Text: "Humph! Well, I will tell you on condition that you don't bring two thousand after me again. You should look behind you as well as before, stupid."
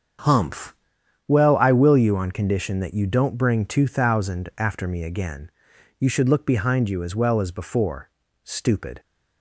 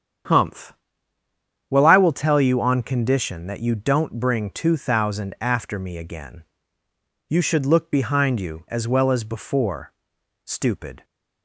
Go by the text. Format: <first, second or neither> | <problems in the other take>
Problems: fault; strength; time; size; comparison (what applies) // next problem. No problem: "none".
second | starts louder than the rest; strong; until 1.7 s; 7.5 dB; strong in the second // skips "tell"; at 1.9 s